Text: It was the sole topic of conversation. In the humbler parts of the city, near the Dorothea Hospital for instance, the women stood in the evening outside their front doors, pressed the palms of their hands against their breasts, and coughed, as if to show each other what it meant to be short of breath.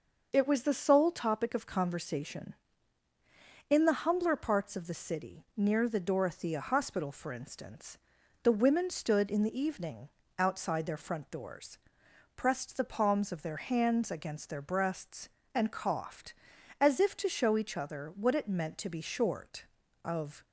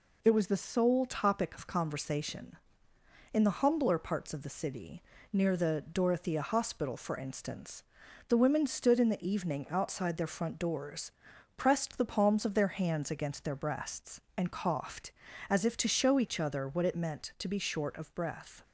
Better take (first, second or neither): second